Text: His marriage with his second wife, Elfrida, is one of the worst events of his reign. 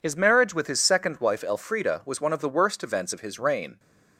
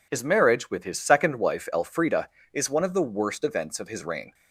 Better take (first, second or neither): second